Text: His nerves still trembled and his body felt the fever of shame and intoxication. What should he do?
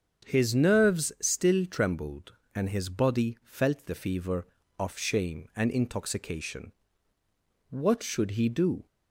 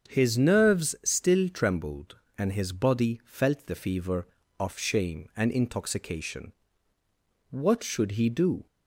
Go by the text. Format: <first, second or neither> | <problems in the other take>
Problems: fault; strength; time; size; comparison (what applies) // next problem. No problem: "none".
neither | starts louder than the rest; strong; the same in both